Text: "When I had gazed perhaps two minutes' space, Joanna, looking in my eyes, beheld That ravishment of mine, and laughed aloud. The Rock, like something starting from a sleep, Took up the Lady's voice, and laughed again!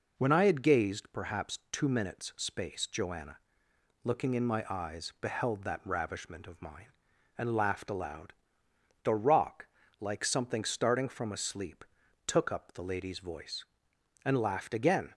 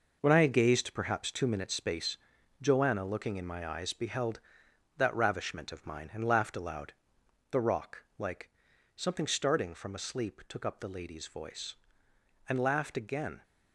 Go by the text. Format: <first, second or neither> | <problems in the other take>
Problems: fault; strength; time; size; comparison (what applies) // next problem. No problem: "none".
first | gets quieter; strong; throughout; 8 dB // pauses between "like" and "something"; noticeable; at 8.4 s; 0.48 s long